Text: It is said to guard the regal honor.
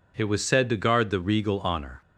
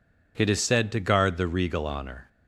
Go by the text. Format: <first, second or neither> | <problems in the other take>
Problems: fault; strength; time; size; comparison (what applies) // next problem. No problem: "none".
second | says "was" for "is"; at 0.2 s